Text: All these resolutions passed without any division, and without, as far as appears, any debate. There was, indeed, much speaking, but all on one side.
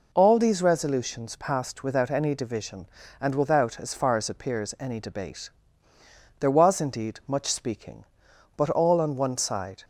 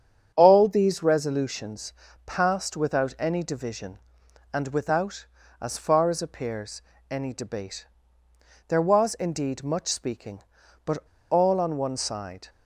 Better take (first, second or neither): first